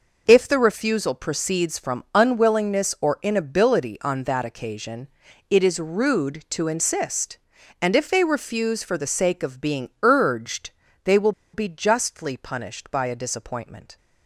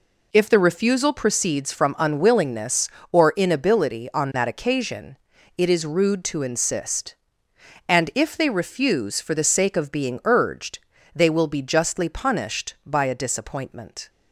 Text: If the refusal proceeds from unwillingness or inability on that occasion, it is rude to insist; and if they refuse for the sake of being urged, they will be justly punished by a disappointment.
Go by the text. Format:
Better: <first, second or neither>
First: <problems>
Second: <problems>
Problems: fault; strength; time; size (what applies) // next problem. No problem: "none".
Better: second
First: pauses between "will" and "be"; slight; at 11.3 s; 0.22 s long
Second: none